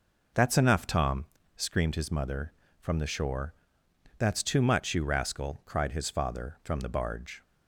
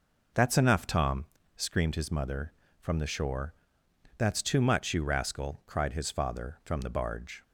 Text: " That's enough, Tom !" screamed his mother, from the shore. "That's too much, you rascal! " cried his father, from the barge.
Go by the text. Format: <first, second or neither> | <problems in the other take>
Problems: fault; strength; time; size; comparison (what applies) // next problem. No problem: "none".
neither | none